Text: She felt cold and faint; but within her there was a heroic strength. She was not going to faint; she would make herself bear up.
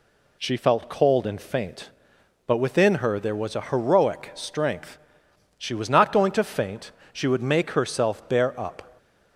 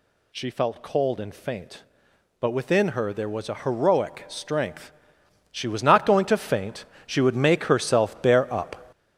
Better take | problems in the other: first | gets louder; throughout; 7 dB

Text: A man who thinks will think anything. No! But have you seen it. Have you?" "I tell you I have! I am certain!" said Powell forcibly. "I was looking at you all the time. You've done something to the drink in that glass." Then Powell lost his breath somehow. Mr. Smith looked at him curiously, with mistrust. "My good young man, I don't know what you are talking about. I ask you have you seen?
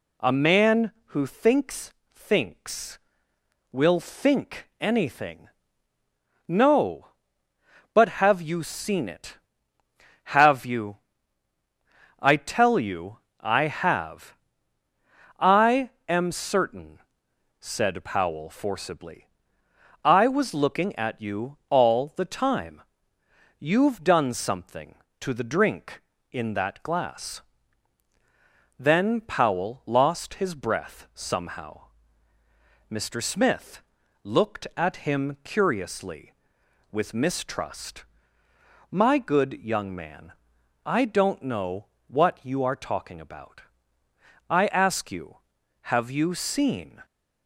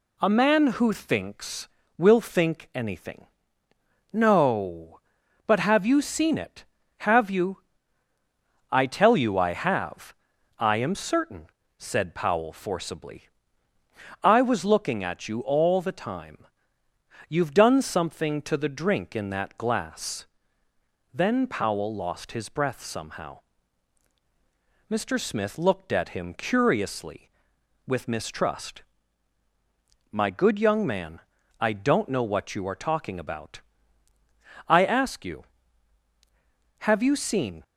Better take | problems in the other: second | says "thinks" twice; at 2.1 s // pauses between "you" and "I"; slight; at 13.1 s; 0.24 s long // pauses between "I" and "am"; slight; at 15.8 s; 0.18 s long // pauses between "Smith" and "looked"; at 33.8 s; 0.44 s long // pauses between "know" and "what"; slight; at 41.8 s; 0.24 s long

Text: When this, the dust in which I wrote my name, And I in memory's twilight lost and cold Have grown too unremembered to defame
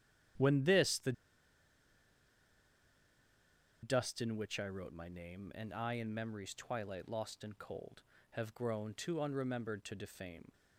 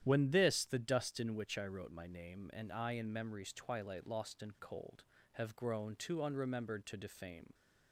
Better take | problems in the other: second | starts louder than the rest; strong; until 4.0 s; 10.5 dB; strong in the second // pauses between "the" and "dust"; strong; at 1.1 s; 2.7 s long

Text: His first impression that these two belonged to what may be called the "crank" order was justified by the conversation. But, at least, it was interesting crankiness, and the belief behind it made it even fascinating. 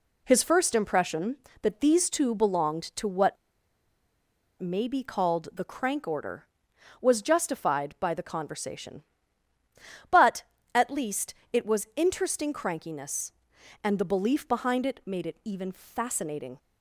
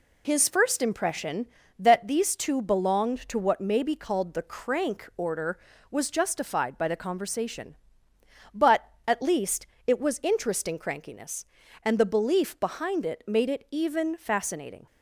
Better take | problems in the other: second | pauses between "what" and "may"; at 3.3 s; 1.2 s long

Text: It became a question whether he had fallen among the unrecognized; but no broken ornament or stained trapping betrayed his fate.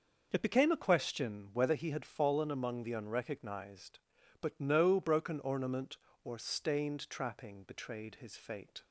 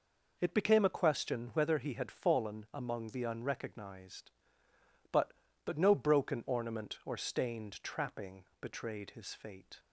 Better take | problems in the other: first | says "but" twice; at 5.6 s // pauses between "trapping" and "betrayed"; slight; at 8.4 s; 0.18 s long

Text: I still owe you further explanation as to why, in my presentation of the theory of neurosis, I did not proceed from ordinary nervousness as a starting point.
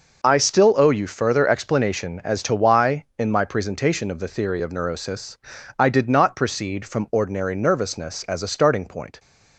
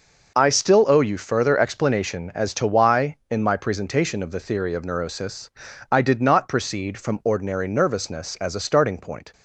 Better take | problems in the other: neither | none

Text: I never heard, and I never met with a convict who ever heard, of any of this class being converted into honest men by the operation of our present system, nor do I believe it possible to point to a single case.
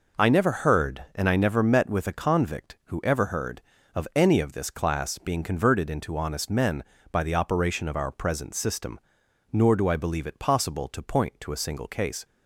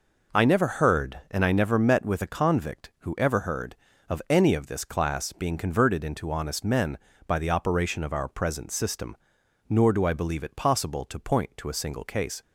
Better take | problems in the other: neither | none

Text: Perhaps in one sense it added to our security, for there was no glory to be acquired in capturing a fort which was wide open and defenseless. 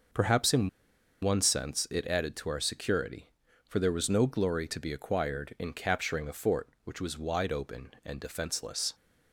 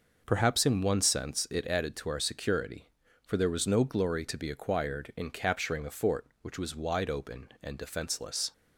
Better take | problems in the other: second | pauses between "in" and "one"; noticeable; at 0.6 s; 0.53 s long

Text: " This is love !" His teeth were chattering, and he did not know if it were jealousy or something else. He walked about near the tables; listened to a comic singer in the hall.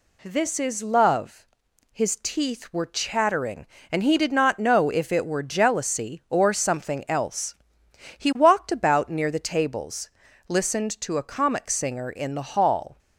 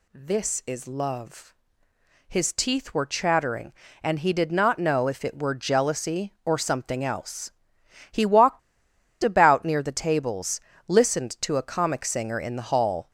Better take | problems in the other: first | pauses between "walked" and "about"; noticeable; at 8.5 s; 0.64 s long

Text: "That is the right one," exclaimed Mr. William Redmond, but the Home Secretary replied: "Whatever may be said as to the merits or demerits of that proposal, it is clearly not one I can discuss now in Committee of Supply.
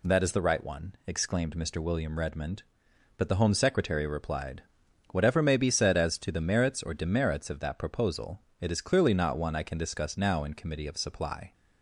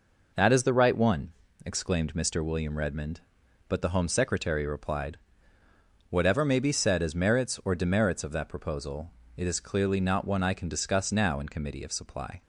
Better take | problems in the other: first | skips "to the"; at 7.1 s

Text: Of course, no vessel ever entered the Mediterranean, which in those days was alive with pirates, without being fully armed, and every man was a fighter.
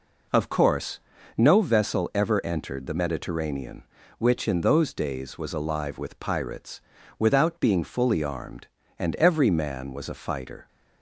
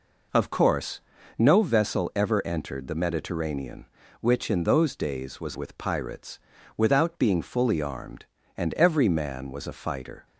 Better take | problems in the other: first | skips "alive"; at 5.5 s

